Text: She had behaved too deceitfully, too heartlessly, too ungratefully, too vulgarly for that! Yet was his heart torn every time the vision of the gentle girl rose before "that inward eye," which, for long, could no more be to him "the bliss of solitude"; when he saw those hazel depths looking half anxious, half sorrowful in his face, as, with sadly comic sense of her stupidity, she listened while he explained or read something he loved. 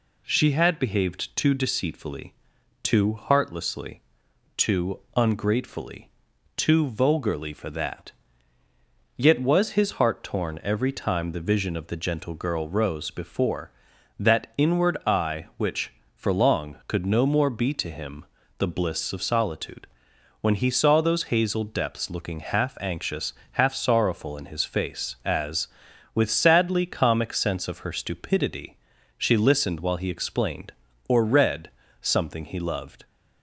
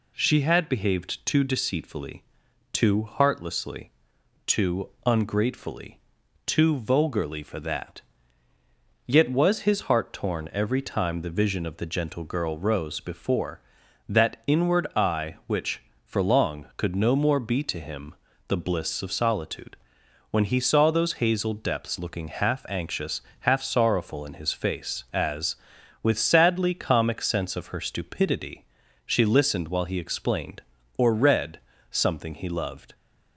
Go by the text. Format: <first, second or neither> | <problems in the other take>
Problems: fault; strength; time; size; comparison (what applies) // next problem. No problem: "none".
neither | pauses between "too" and "ungratefully"; slight; the same in both // pauses between "him" and "the"; slight; the same in both // pauses between "read" and "something"; slight; the same in both